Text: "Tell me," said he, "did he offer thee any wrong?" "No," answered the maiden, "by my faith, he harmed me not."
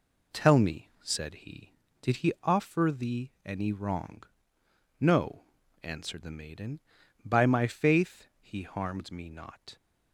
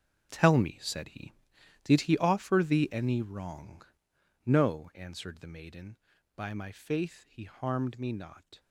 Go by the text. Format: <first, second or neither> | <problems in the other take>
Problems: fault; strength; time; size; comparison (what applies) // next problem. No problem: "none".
first | gets quieter; strong; throughout; 15 dB